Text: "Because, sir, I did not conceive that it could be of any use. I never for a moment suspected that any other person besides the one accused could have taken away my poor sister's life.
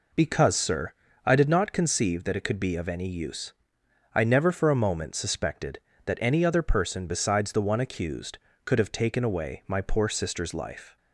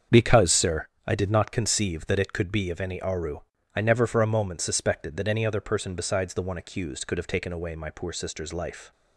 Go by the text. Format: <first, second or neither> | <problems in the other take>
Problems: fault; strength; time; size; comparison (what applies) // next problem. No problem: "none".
first | starts louder than the rest; until 1.3 s; 7 dB // says "aru" for "use"; at 3.0 s